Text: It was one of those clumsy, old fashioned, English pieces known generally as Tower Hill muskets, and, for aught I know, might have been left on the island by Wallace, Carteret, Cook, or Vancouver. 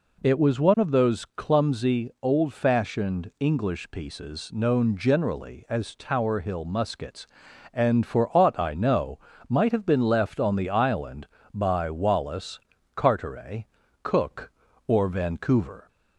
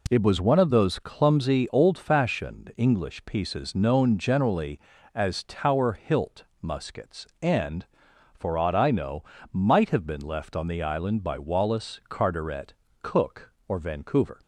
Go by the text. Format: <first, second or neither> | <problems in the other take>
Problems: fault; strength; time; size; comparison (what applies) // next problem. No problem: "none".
first | says "Hilt" for "Hill"; at 5.9 s